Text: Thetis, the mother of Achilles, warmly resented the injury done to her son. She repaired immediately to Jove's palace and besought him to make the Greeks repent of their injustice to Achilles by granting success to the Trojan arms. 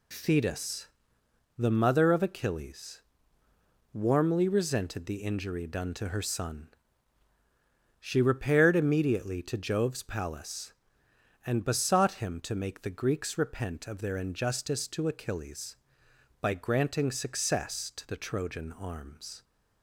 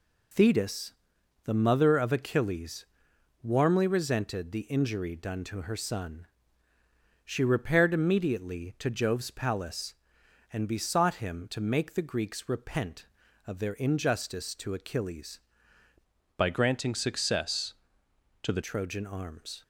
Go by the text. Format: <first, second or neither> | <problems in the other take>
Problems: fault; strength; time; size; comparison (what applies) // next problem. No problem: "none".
first | changes voice from "by" to "the"; from 16.3 to 18.6 s; 2.3 s long